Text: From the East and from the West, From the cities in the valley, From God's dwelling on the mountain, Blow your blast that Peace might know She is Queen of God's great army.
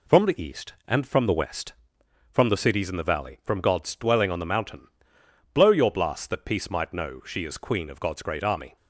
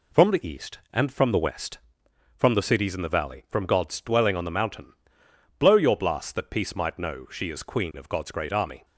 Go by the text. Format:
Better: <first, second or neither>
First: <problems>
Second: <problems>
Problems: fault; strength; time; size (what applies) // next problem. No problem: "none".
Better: neither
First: none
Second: none